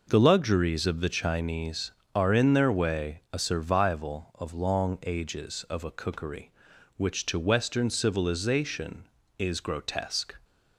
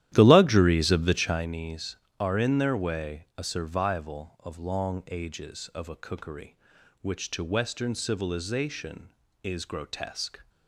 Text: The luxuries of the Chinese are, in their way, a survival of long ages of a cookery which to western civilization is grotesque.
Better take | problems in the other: first | starts louder than the rest; strong; until 1.5 s; 12.5 dB

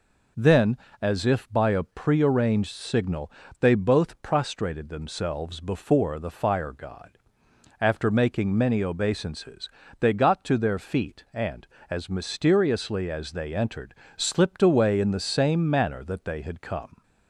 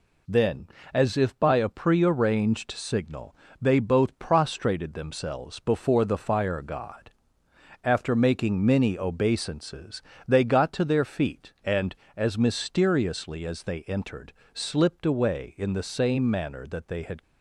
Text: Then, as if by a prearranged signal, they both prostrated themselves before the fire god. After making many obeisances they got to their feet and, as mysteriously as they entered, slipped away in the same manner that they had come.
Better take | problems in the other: first | pauses between "obeisances" and "they"; slight; at 10.0 s; 0.24 s long; slight in the first // stops before "come"; at 17.2 s

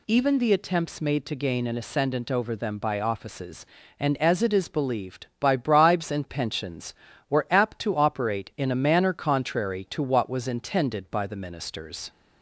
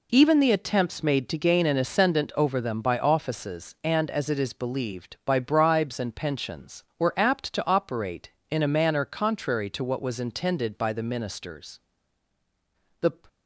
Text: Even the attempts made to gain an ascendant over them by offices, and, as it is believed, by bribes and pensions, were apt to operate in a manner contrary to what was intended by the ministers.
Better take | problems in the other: first | goes on to say "The"; slight; from 12.9 s on; 0.14 s long

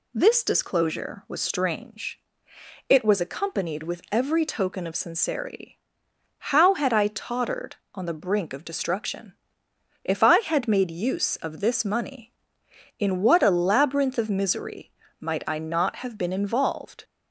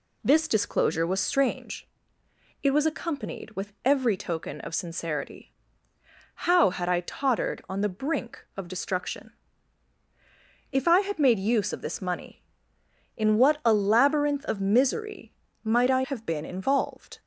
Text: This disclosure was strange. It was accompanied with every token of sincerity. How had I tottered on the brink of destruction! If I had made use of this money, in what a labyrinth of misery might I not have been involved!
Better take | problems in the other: first | pauses between "misery" and "might"; slight; at 15.3 s; 0.32 s long; slight in the first // skips "not"; at 16.0 s

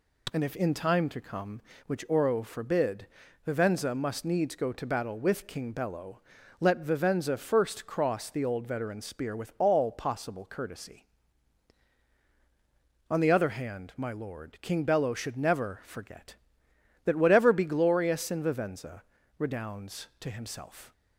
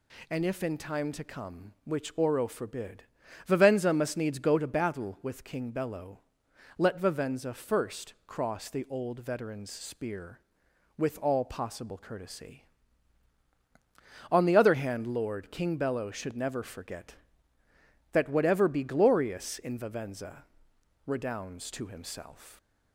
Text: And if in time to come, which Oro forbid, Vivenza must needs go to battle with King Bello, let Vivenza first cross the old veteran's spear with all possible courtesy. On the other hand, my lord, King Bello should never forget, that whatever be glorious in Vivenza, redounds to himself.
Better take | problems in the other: first | skips "my"; at 15.0 s

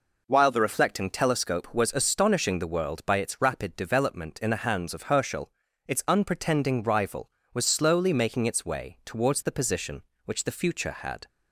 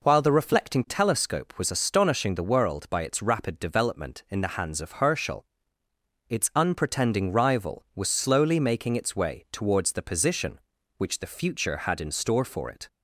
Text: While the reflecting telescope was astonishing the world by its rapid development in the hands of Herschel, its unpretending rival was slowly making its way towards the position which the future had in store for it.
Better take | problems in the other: second | stops before "in store for it"; at 11.2 s

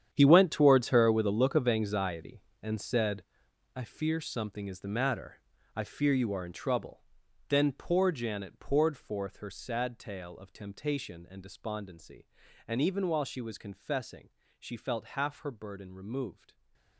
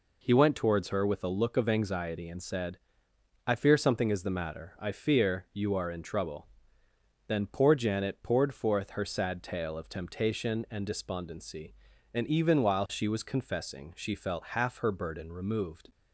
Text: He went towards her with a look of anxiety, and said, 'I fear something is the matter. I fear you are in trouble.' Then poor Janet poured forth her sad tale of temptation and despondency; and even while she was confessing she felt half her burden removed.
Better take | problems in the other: second | gets quieter; strong; throughout; 14 dB // pauses between "confessing" and "she"; slight; at 14.2 s; 0.30 s long

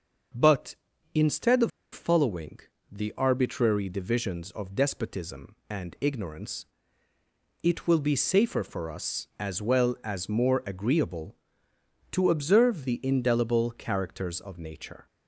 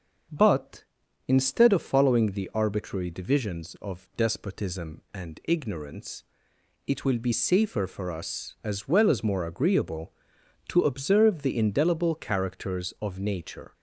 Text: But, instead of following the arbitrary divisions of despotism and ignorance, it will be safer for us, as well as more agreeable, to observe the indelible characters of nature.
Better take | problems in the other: second | starts louder than the rest; until 1.9 s; 6.5 dB; also in the second // pauses between "of" and "following"; slight; at 1.7 s; 0.23 s long // pauses between "following" and "the"; slight; at 2.5 s; 0.30 s long

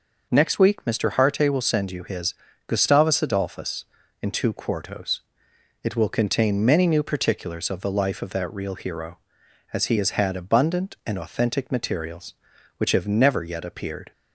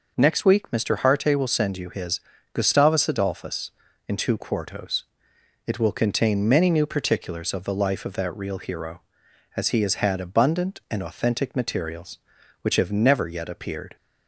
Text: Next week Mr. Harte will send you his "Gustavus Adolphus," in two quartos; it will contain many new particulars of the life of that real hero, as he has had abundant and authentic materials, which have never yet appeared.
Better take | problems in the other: neither | pauses between "his" and "Gustavus"; slight; the same in both

